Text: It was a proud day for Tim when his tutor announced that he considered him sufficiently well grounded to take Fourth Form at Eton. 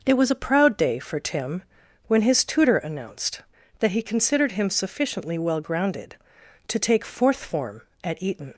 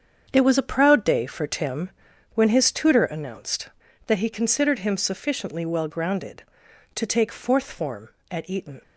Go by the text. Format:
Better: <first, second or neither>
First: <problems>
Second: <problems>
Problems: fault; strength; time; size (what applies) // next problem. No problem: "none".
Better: first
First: pauses between "Tim" and "when"; at 1.6 s; 0.44 s long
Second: gets quieter; strong; throughout; 10.5 dB // pauses between "Tim" and "when"; at 1.8 s; 0.44 s long